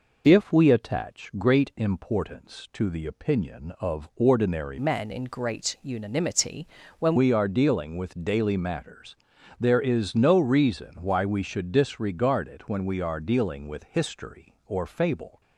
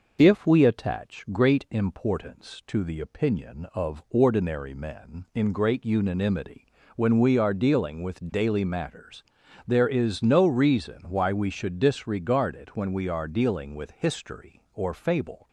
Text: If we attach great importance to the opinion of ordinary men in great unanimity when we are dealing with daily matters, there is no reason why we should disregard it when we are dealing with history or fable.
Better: second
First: changes voice from "men" to "when"; from 4.7 to 7.1 s; 2.4 s long // pauses between "unanimity" and "when"; slight; at 6.6 s; 0.36 s long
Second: pauses between "unanimity" and "when"; slight; at 6.6 s; 0.30 s long

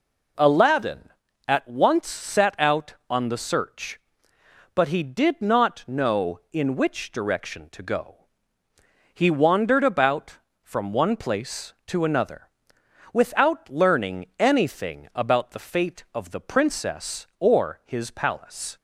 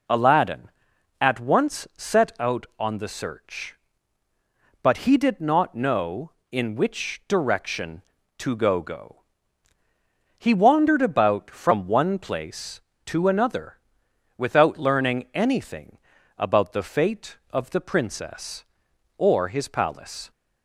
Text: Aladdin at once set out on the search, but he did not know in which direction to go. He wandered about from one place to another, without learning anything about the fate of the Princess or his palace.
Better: first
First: none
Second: says "go" twice; at 8.8 s // pauses between "anything" and "about"; at 15.9 s; 0.38 s long

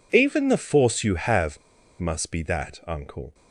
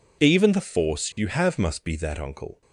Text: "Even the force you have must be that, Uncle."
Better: second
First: pauses between "have" and "must"; at 1.5 s; 0.41 s long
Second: none

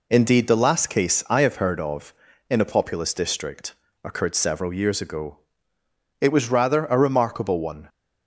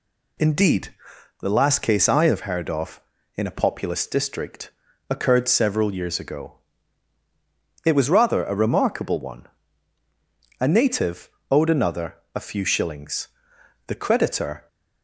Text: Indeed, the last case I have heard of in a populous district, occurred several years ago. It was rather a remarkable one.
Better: first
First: none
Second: goes on to say "A native owed another a few shillings the creditor"; strong; from 10.5 s on; 4.0 s long

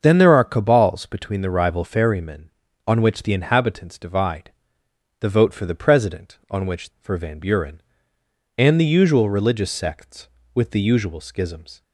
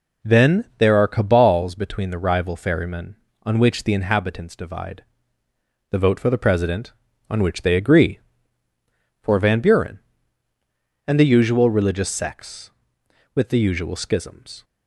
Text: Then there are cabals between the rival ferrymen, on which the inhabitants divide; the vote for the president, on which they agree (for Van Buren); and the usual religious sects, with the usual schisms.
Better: second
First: starts louder than the rest; until 1.0 s; 6.5 dB // skips "they agree"; at 6.9 s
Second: none

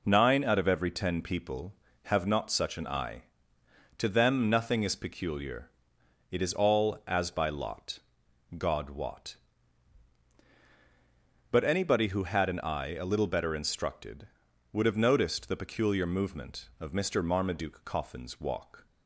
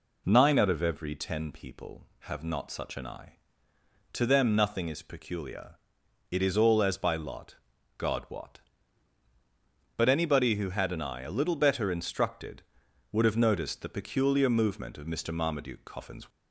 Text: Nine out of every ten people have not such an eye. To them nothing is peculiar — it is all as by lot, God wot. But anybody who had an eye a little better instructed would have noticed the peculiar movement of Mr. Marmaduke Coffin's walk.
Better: first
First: none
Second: stops before "walk"; at 16.3 s

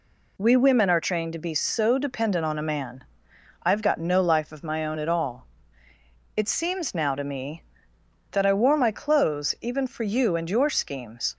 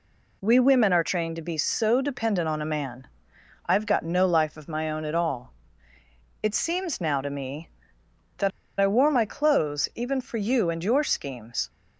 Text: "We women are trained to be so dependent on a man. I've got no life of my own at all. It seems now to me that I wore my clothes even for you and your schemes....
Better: first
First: none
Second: pauses between "that" and "I"; slight; at 8.5 s; 0.30 s long

